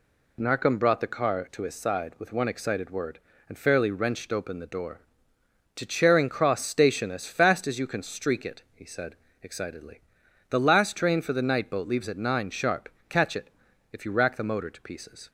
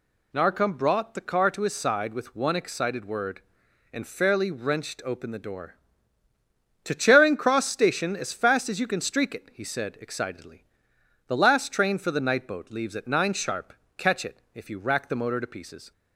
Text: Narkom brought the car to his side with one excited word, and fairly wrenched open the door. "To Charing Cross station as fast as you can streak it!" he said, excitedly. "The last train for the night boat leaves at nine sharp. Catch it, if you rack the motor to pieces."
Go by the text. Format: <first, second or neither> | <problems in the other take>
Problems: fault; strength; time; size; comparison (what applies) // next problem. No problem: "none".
neither | none